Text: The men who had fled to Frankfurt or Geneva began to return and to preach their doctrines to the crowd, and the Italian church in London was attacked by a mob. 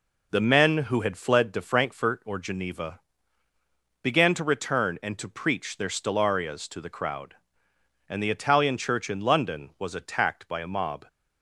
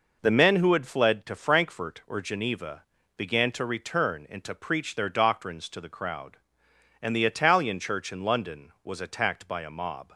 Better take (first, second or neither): second